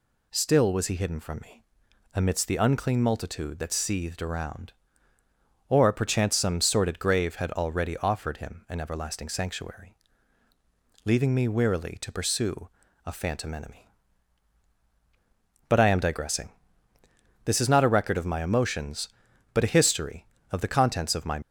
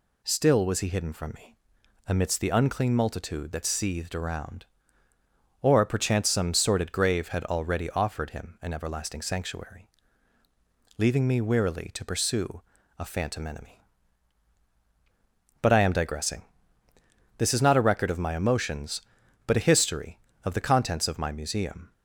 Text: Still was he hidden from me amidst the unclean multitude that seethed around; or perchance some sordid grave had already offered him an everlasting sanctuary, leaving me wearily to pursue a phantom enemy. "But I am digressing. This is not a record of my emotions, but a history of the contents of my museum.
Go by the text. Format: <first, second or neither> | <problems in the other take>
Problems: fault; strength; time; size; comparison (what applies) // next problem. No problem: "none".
second | pauses between "me" and "amidst"; noticeable; at 1.6 s; 0.52 s long; noticeable in the second // pauses between "pursue" and "a"; at 12.6 s; 0.38 s long; also in the second // stops before "museum"; at 21.4 s